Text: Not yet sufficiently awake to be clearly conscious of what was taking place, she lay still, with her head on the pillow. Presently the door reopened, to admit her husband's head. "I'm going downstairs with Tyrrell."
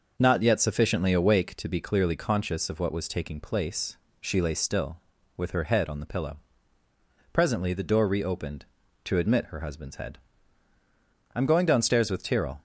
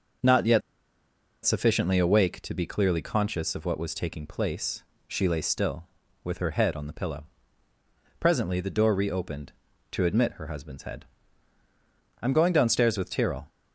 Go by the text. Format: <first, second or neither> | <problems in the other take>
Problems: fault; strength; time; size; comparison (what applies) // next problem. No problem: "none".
first | starts louder than the rest; noticeable; until 2.0 s; 6 dB; noticeable in the first // pauses between "yet" and "sufficiently"; noticeable; at 0.6 s; 0.83 s long